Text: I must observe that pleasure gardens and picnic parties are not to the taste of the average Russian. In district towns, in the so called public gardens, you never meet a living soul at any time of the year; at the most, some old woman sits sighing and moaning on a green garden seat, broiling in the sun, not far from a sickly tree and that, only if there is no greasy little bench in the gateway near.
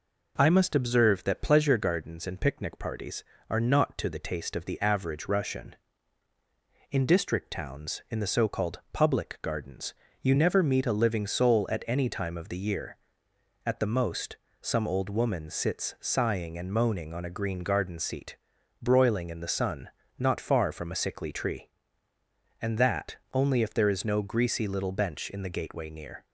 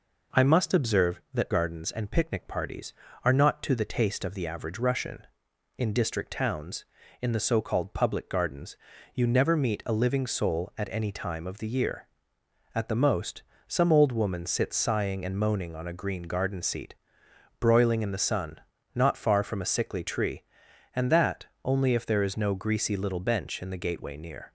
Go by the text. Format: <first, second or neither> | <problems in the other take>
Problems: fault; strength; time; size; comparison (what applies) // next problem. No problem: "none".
first | skips "pleasure"; at 1.5 s